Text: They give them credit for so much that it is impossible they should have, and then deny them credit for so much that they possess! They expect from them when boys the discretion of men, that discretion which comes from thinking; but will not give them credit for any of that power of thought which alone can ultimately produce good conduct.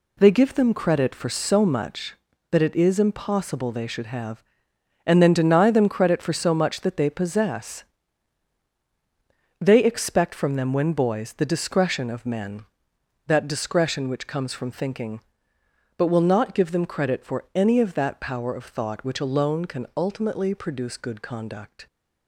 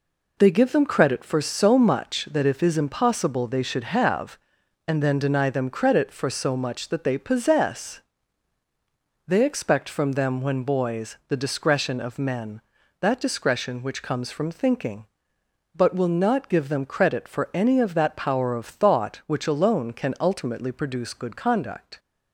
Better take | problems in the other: first | says "if" for "it"; at 2.4 s

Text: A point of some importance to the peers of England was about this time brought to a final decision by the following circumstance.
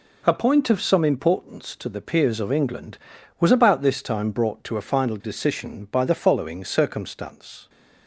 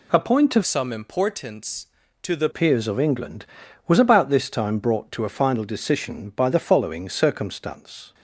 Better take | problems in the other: first | changes voice from "some" to "the"; from 0.6 to 2.4 s; 1.8 s long

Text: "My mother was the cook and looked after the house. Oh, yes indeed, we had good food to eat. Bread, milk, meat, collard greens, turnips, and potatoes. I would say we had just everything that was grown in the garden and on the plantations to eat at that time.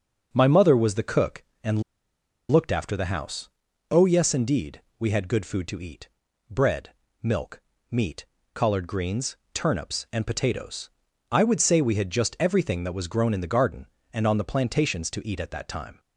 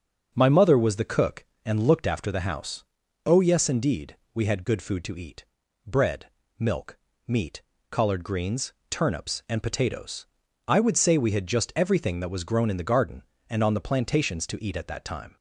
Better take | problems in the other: second | starts louder than the rest; until 1.3 s; 6.5 dB; also in the second // pauses between "and" and "looked"; noticeable; at 1.8 s; 0.68 s long

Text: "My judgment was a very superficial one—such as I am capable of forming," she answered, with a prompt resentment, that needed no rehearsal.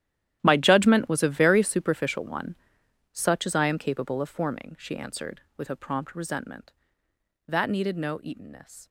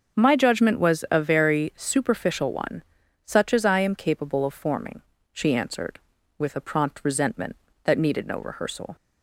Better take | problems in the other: second | starts louder than the rest; strong; until 1.4 s; 11.5 dB; also in the second // says "eatenness" for "rehearsal"; at 8.2 s

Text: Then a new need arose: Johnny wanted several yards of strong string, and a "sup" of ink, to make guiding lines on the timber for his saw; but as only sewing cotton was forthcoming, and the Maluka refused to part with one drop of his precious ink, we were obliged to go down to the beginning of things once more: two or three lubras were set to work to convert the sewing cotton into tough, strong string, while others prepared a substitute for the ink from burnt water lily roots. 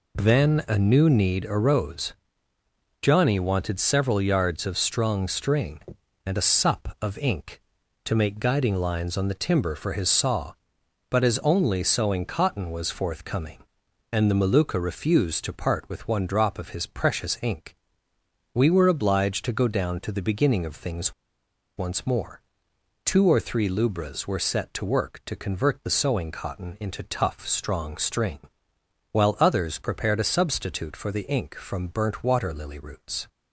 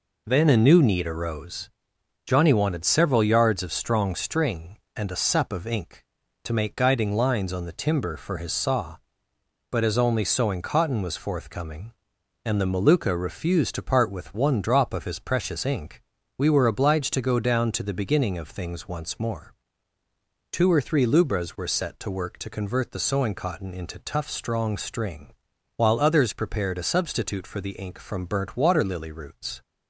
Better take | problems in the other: second | pauses between "things" and "once"; noticeable; at 21.1 s; 0.64 s long

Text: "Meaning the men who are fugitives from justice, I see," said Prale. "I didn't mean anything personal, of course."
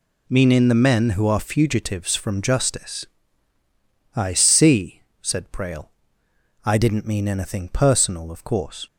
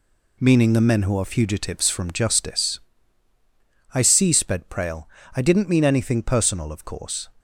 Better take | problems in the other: first | says "sped" for "said"; at 4.3 s

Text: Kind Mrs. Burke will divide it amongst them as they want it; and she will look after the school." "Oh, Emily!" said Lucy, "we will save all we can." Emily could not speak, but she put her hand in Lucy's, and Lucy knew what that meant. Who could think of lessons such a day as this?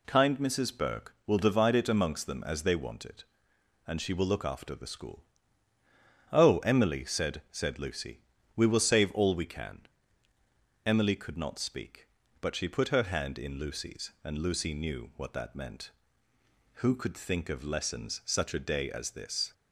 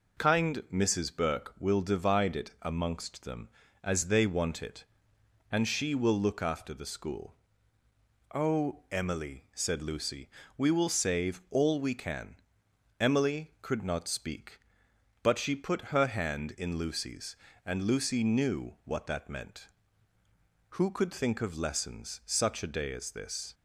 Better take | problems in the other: second | says "said" twice; at 7.5 s

